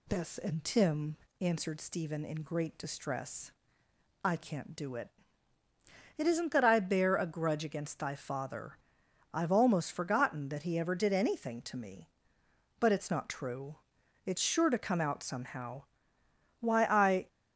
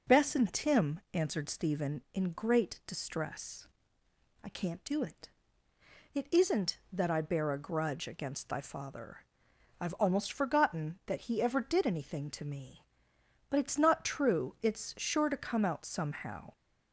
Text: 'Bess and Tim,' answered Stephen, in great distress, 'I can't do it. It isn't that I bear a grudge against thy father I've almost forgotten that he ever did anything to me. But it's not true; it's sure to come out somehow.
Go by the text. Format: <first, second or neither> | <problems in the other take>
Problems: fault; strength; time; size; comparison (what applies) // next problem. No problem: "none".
second | pauses between "father" and "I've"; noticeable; at 8.7 s; 0.56 s long; noticeable in the second // goes on to say "Why I"; noticeable; from 16.6 s on; 0.64 s long